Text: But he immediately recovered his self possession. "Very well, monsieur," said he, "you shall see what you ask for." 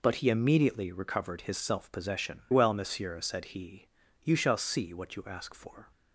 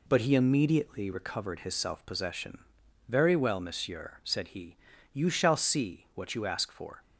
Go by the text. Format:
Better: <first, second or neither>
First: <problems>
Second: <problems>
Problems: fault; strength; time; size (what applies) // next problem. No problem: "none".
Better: second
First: skips "Very"; at 2.4 s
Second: none